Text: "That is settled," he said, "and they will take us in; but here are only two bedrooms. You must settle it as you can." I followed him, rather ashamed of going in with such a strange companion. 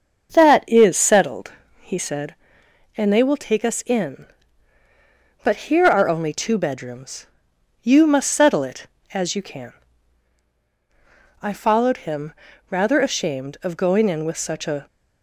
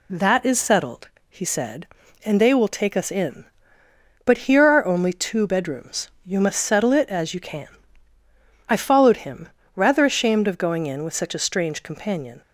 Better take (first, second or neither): second